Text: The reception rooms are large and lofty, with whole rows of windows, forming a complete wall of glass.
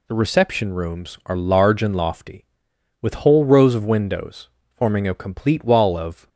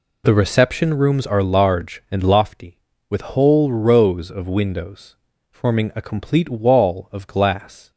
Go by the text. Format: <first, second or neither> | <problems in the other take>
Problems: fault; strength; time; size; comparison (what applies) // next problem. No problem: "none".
second | stops before "glass"; at 6.2 s